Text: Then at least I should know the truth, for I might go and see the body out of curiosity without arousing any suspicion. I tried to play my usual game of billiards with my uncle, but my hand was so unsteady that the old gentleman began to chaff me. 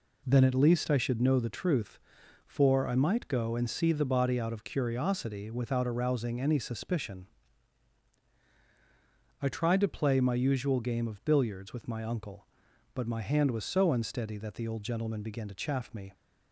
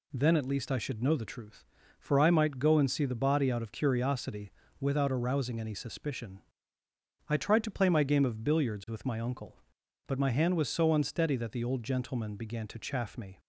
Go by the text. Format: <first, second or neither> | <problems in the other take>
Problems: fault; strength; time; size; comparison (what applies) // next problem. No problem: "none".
first | pauses between "curiosity" and "without"; slight; at 4.5 s; 0.28 s long // skips "usual"; at 8.0 s